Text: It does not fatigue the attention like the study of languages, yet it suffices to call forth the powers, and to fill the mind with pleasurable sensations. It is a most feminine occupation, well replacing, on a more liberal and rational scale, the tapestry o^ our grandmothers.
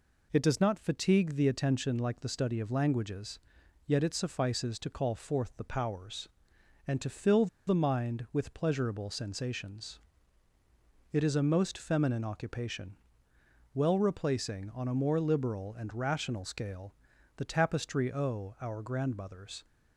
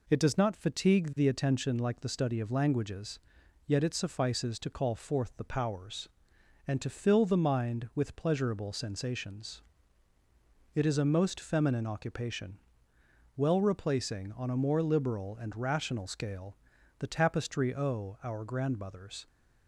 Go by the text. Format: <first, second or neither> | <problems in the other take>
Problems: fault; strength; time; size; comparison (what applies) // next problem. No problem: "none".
second | pauses between "fill" and "the"; slight; at 7.4 s; 0.20 s long